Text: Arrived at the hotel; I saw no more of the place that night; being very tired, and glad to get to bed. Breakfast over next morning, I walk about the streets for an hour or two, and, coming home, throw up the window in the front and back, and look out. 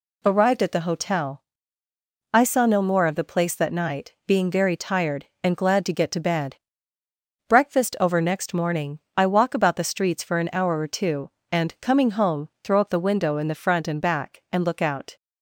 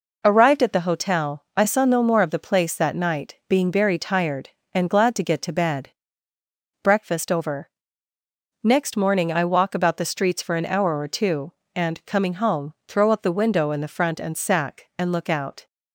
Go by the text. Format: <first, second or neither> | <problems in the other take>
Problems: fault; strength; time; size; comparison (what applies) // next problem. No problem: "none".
first | pauses between "over" and "next"; noticeable; at 7.6 s; 0.94 s long // says "sack" for "back"; at 14.3 s